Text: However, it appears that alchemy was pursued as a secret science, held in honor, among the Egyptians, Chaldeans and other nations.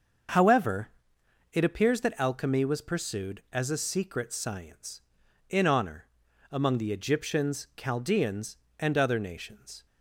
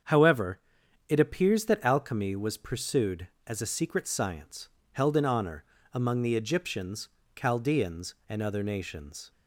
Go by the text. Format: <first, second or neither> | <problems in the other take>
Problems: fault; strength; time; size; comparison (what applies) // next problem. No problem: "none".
second | starts louder than the rest; until 1.9 s; 6.5 dB; strong in the second // skips "held"; at 5.2 s